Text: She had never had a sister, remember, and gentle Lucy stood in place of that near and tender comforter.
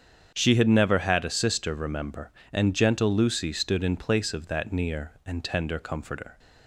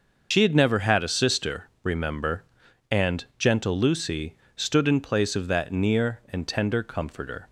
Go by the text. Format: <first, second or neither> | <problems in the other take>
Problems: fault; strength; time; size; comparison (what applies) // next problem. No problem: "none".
first | loses the start of "She"; at 0.3 s; 70 ms // starts louder than the rest; noticeable; until 1.3 s; 6 dB; strong in the first // pauses between "Lucy" and "stood"; slight; at 4.3 s; 0.20 s long